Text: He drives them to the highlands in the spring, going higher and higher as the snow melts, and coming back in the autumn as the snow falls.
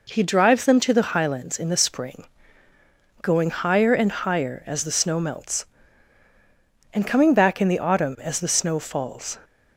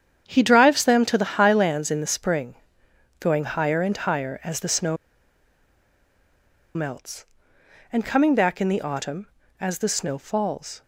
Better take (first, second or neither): first